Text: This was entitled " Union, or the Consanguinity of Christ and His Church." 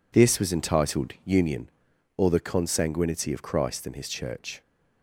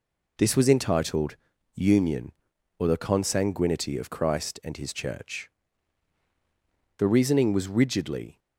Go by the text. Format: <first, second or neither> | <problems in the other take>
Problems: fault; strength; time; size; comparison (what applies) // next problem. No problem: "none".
first | goes on to say "The reasoning was rigidly"; from 6.9 s on; 1.4 s long